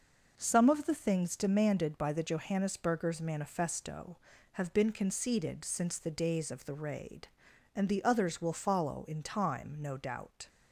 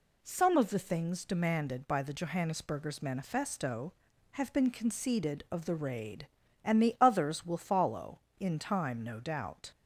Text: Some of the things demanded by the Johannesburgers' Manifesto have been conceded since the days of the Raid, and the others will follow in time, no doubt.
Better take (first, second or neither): first